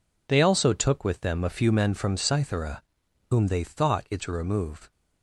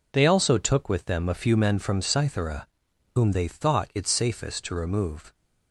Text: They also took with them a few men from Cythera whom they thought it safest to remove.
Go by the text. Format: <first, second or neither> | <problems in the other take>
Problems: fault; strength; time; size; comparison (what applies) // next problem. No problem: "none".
second | pauses between "Cythera" and "whom"; noticeable; at 2.8 s; 0.48 s long; noticeable in the second // skips "safest"; at 4.2 s